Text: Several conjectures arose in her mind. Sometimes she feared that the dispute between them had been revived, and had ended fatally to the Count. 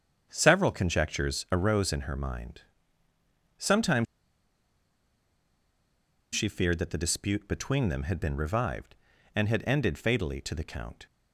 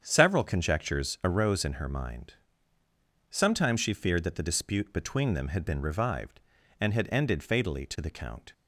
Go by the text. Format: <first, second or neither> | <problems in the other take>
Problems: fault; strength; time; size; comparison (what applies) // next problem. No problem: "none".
second | starts louder than the rest; strong; until 1.3 s; 7.5 dB; strong in the second // pauses between "Sometimes" and "she"; strong; at 4.0 s; 2.2 s long